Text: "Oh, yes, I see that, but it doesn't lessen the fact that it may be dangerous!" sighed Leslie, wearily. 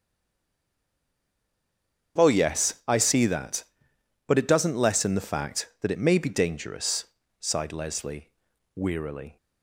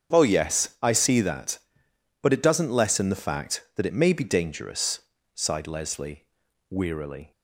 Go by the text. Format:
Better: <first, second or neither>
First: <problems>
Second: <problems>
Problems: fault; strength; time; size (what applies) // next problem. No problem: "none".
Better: second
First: stays silent before the first word; until 2.1 s; 2.1 s long // starts louder than the rest; strong; until 3.2 s; 7 dB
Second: starts louder than the rest; strong; until 1.1 s; 7 dB